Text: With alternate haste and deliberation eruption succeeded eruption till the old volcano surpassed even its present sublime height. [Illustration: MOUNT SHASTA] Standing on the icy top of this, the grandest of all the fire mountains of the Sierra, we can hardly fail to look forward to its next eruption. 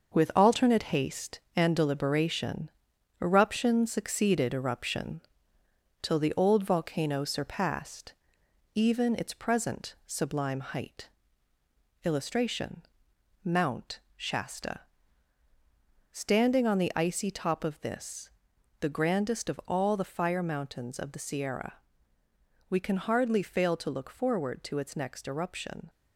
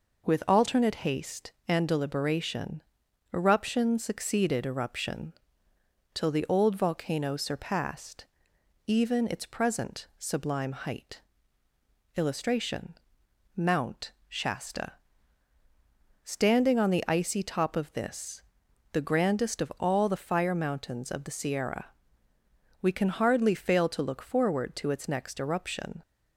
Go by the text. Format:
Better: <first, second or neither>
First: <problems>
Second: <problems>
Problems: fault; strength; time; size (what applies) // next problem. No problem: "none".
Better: second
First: gets quieter; noticeable; throughout; 6 dB // pauses between "deliberation" and "eruption"; noticeable; at 2.6 s; 0.50 s long // pauses between "eruption" and "till"; noticeable; at 5.2 s; 0.80 s long // pauses between "surpassed" and "even"; noticeable; at 8.1 s; 0.62 s long // pauses between "MOUNT" and "SHASTA"; slight; at 14.0 s; 0.16 s long // pauses between "SHASTA" and "Standing"; strong; at 14.8 s; 1.3 s long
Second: pauses between "deliberation" and "eruption"; noticeable; at 2.8 s; 0.50 s long // pauses between "eruption" and "till"; noticeable; at 5.3 s; 0.80 s long // pauses between "surpassed" and "even"; noticeable; at 8.2 s; 0.62 s long // pauses between "MOUNT" and "SHASTA"; slight; at 14.1 s; 0.16 s long // pauses between "SHASTA" and "Standing"; strong; at 14.9 s; 1.3 s long